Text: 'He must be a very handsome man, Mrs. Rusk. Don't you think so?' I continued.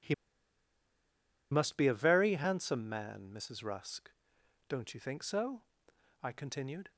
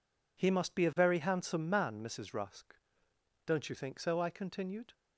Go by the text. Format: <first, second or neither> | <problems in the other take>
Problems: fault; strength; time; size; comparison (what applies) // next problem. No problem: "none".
second | pauses between "He" and "must"; strong; at 0.1 s; 1.3 s long